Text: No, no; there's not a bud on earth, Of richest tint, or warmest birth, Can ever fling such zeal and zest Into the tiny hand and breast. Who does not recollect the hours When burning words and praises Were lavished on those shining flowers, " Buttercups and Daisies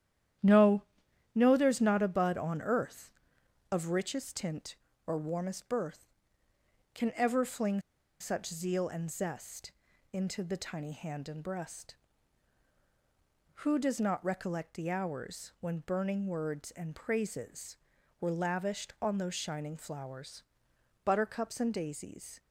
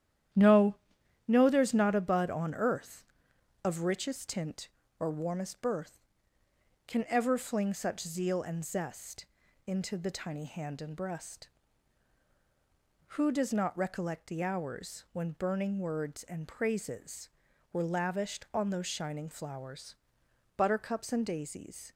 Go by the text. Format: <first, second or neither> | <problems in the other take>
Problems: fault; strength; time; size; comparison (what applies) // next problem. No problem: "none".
second | starts louder than the rest; strong; until 1.9 s; 11 dB; strong in the second // pauses between "fling" and "such"; at 7.8 s; 0.39 s long // pauses between "zest" and "Into"; at 9.7 s; 0.40 s long; also in the second